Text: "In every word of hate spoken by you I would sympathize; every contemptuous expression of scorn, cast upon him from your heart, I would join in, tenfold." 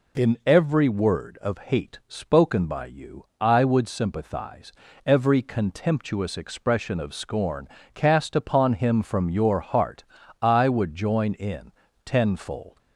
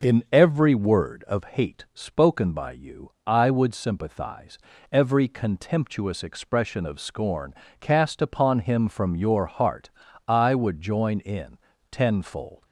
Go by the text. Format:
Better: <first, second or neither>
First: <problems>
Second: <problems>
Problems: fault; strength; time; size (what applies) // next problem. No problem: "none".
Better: first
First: none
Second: starts louder than the rest; noticeable; until 1.5 s; 5.5 dB